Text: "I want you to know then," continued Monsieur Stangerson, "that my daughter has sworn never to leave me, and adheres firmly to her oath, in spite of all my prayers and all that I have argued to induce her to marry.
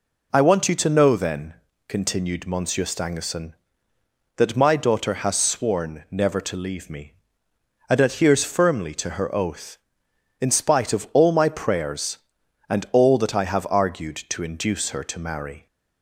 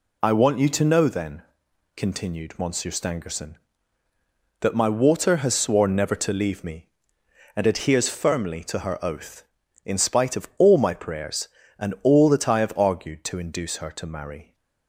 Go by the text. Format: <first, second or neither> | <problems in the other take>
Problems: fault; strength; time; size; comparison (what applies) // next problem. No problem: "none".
first | says "water" for "daughter"; at 4.8 s